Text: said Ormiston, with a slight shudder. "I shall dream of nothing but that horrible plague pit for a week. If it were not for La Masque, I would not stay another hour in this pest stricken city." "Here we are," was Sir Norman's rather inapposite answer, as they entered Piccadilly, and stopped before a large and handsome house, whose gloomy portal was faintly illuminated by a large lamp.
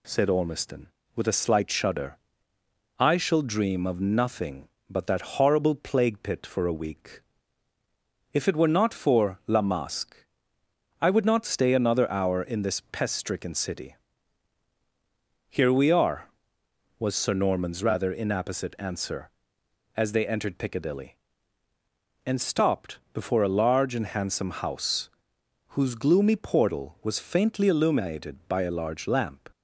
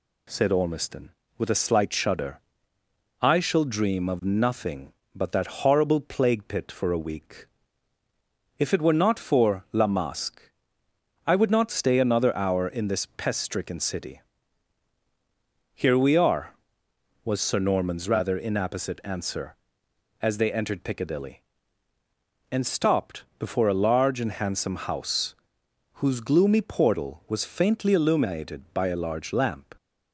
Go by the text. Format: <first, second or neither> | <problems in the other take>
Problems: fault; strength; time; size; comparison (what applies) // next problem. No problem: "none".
neither | pauses between "stopped" and "before"; slight; the same in both